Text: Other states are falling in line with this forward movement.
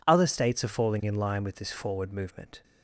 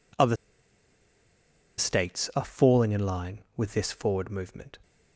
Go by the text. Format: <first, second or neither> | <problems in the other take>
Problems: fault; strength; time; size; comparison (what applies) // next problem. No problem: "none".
first | pauses between "Other" and "states"; strong; at 0.3 s; 1.4 s long